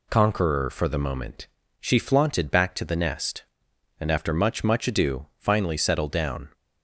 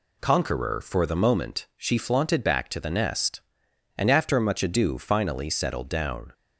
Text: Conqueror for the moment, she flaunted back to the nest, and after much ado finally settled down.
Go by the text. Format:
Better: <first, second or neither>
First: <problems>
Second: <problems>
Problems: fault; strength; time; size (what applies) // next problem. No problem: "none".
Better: second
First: says "much" twice; at 4.6 s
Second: none